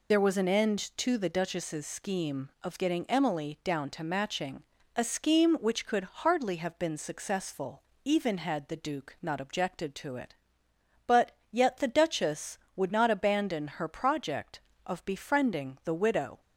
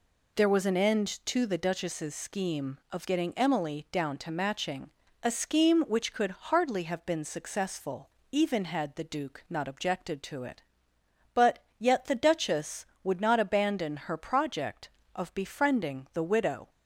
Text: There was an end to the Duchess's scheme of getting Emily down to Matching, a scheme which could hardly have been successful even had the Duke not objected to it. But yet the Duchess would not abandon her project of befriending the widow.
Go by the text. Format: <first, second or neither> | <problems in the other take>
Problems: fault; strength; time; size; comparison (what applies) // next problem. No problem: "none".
second | loses the start of "There"; at 0.1 s; 40 ms // pauses between "successful" and "even"; slight; at 7.8 s; 0.22 s long; slight in the second // pauses between "But" and "yet"; slight; at 11.3 s; 0.20 s long; slight in the second